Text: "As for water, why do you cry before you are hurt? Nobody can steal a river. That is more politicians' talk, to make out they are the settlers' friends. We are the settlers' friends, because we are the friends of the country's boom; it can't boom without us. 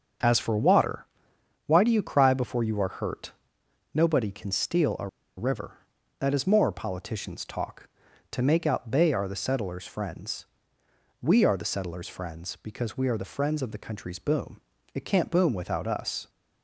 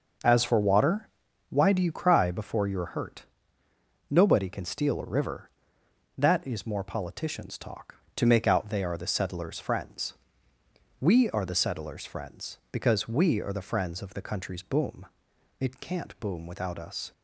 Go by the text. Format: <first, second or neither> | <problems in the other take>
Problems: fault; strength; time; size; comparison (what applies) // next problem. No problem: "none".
second | starts louder than the rest; until 1.8 s; 7 dB // pauses between "a" and "river"; slight; at 5.0 s; 0.29 s long